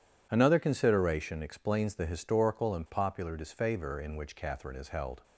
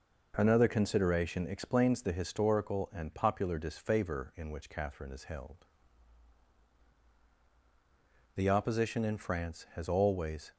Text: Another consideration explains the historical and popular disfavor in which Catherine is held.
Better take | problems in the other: first | goes on to say "The Opposition in France has always"; strong; from 8.3 s on; 2.1 s long

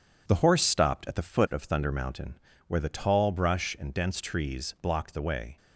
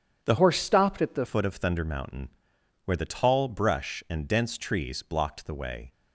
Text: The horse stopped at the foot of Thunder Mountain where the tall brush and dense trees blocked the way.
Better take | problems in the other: first | starts louder than the rest; strong; until 1.2 s; 8 dB // changes voice from "horse" to "the"; from 0.3 to 1.2 s; 0.9 s long // pauses between "Mountain" and "where"; noticeable; at 2.2 s; 0.56 s long; slight in the first

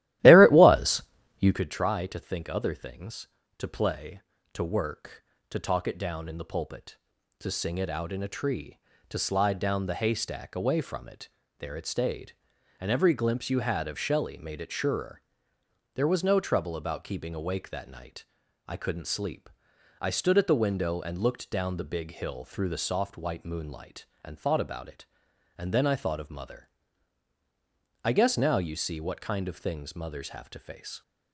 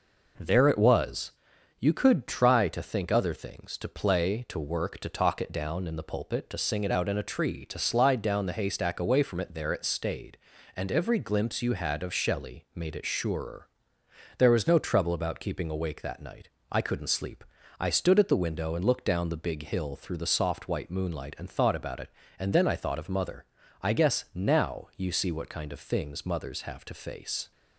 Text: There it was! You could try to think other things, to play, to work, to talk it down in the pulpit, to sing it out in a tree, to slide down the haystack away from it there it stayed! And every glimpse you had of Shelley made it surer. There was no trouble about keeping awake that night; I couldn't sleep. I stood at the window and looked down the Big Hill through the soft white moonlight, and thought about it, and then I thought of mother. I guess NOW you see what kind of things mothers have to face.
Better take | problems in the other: second | starts louder than the rest; strong; until 1.7 s; 15 dB // pauses between "it" and "there"; slight; at 11.2 s; 0.32 s long

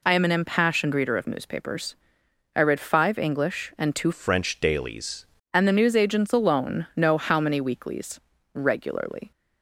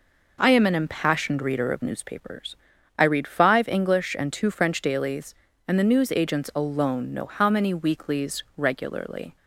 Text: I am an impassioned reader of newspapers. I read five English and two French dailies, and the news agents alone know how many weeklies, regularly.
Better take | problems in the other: second | changes voice from "French" to "dailies"; from 4.1 to 5.2 s; 1.1 s long

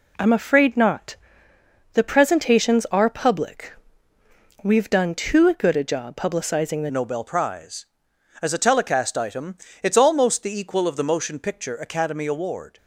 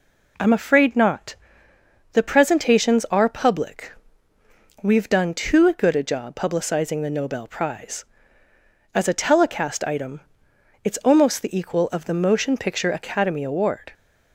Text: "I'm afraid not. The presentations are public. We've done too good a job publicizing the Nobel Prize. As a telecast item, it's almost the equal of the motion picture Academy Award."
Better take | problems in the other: second | changes voice at "Nobel"; from 6.9 s on; 5.8 s long

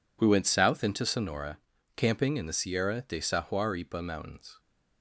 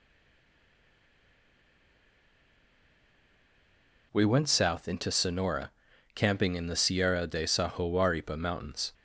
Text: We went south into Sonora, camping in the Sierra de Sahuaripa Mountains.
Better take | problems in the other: first | stays silent before the first word; strong; until 4.1 s; 4.1 s long

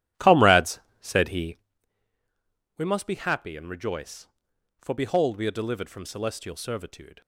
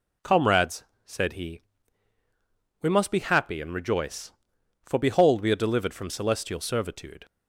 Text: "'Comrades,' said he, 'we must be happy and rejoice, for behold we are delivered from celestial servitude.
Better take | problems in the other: second | starts louder than the rest; strong; until 1.7 s; 12 dB

